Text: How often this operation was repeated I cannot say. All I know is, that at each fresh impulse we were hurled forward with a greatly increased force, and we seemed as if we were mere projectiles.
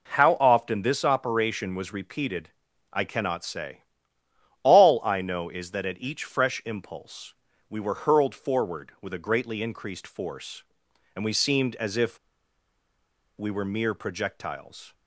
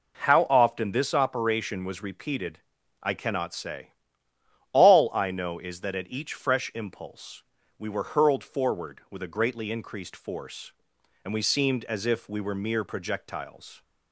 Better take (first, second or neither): second